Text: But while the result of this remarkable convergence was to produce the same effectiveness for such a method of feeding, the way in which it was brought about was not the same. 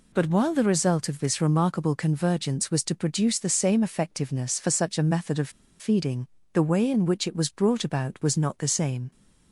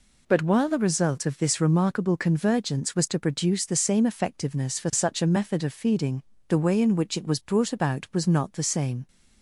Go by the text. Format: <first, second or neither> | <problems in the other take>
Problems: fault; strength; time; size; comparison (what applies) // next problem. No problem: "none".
second | pauses between "of" and "feeding"; slight; at 5.4 s; 0.30 s long